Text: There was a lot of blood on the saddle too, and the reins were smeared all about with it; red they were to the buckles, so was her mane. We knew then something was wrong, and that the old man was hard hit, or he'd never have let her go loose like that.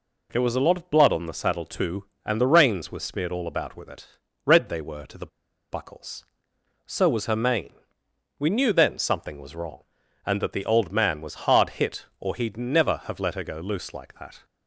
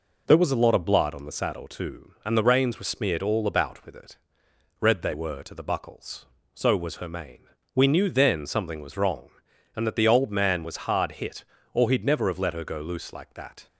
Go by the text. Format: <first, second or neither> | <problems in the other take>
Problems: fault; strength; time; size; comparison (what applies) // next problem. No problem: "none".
second | pauses between "the" and "buckles"; at 5.2 s; 0.44 s long